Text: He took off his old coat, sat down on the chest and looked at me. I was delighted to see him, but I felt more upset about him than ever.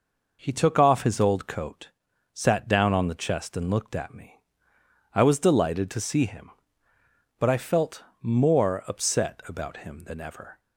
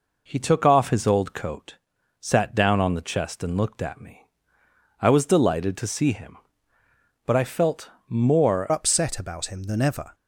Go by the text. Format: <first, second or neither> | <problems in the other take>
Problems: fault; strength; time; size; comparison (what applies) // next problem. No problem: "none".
first | pauses between "felt" and "more"; slight; at 7.9 s; 0.16 s long; slight in the first // changes voice at "upset"; from 8.7 s on; 1.4 s long